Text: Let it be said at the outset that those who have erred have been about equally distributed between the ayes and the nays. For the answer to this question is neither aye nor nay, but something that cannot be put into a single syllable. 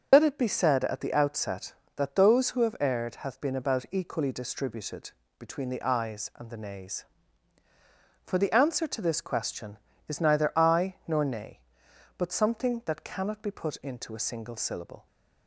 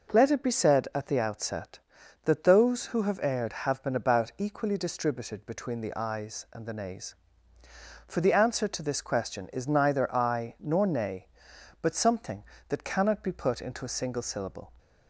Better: second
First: loses the start of "Let"; at 0.1 s; 65 ms // starts louder than the rest; until 1.1 s; 6.5 dB // pauses between "distributed" and "between"; slight; at 5.1 s; 0.26 s long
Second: none

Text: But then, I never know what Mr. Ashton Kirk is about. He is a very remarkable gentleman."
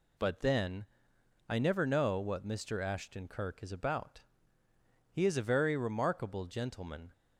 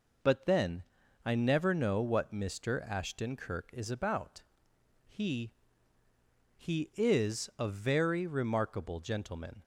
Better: first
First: none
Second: says "He" twice; at 6.5 s

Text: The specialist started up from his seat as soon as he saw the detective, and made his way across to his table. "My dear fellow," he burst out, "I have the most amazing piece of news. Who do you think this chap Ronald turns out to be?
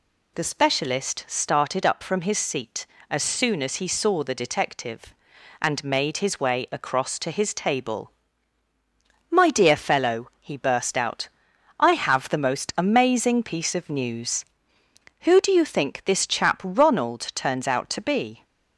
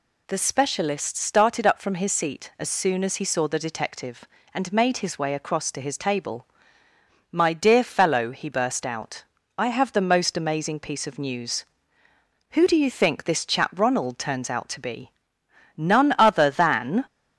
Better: first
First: none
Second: goes on to say "None other than"; noticeable; from 15.7 s on; 1.2 s long

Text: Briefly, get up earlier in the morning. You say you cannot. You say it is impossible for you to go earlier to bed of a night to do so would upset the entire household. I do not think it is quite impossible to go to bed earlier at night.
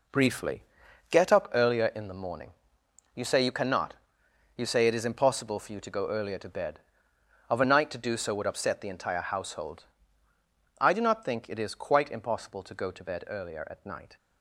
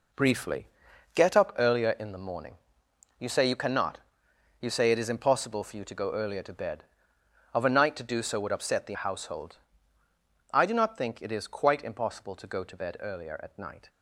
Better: first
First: none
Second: skips "entire"; at 8.9 s

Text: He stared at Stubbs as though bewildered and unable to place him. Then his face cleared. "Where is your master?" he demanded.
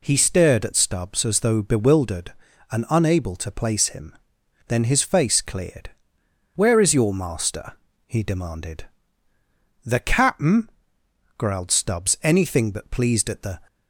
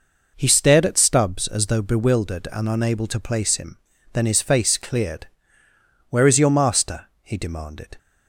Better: second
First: goes on to say "The cap'n growled Stubbs anything but pleased at the"; strong; from 9.8 s on; 3.7 s long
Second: none

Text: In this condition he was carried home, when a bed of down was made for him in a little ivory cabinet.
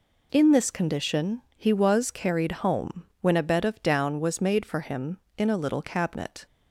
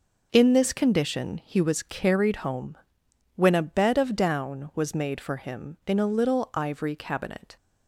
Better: second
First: pauses between "condition" and "he"; slight; at 1.4 s; 0.16 s long // skips "ivory"; at 5.8 s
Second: none

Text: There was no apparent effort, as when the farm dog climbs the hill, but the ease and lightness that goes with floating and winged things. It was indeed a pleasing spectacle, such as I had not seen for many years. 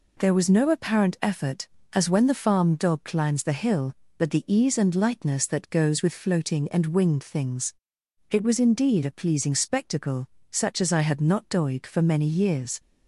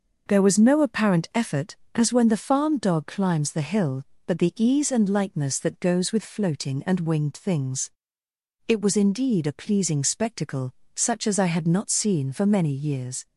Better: second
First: says "doig" for "seen"; at 11.4 s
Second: none

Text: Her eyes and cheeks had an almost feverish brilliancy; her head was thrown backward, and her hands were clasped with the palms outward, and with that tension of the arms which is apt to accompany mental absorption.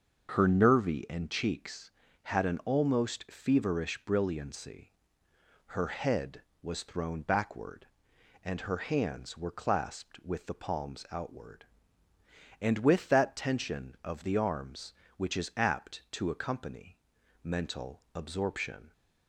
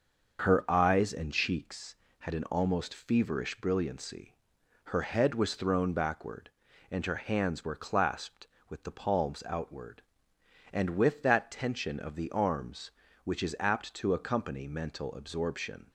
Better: second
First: starts louder than the rest; until 1.3 s; 6.5 dB // says "nervy" for "eyes"; at 0.4 s // pauses between "accompany" and "mental"; at 16.9 s; 0.42 s long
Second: starts louder than the rest; until 1.4 s; 6.5 dB

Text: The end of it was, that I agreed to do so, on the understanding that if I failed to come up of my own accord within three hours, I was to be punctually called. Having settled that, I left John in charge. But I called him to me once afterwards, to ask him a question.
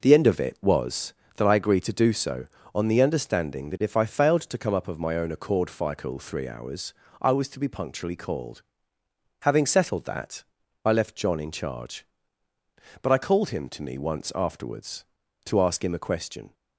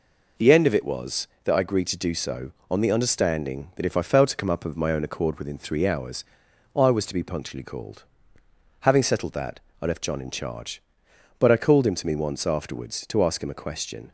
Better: second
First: says "fical" for "within"; at 5.6 s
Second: none

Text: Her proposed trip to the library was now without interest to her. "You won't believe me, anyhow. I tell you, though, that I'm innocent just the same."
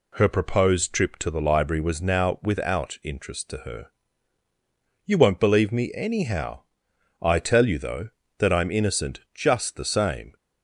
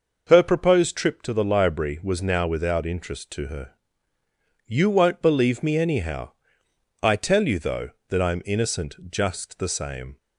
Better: neither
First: none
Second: none

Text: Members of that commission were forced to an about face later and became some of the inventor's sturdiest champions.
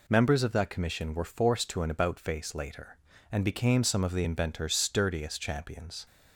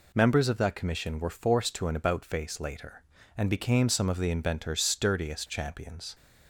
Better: neither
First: none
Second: none

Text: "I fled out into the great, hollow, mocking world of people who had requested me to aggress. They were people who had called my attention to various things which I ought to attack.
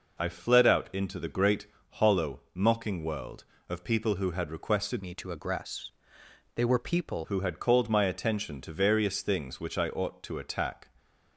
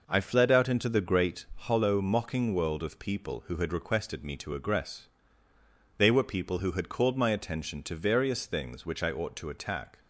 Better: second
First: changes voice from "me" to "people"; from 5.0 to 7.2 s; 2.2 s long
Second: none

